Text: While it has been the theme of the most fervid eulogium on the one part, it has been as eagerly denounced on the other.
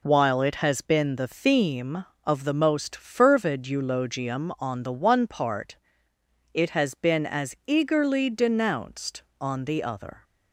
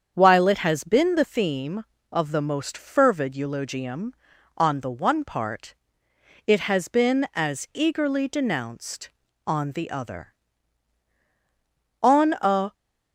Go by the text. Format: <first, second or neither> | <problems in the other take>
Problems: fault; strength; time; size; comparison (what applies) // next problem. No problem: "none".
first | starts louder than the rest; strong; until 1.1 s; 7.5 dB // goes on to say "On a"; noticeable; from 12.0 s on; 0.74 s long